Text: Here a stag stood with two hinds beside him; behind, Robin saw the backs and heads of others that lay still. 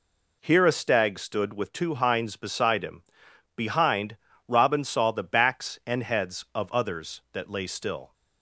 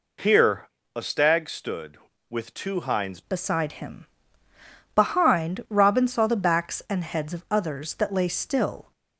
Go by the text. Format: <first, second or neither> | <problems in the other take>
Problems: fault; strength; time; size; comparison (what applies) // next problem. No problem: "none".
first | pauses between "Here" and "a"; slight; at 0.6 s; 0.28 s long // changes voice at "beside"; from 3.2 s on; 5.7 s long